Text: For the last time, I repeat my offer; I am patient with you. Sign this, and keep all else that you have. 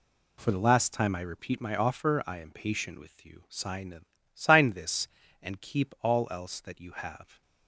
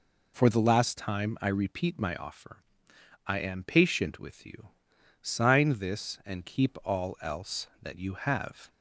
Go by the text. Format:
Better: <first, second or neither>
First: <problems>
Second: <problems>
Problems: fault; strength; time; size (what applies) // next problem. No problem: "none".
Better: second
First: says "Sign" twice; at 4.3 s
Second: none